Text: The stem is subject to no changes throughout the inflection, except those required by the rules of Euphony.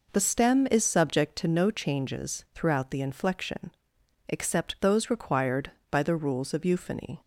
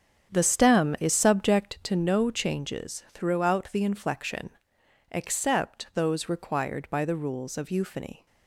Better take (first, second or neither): first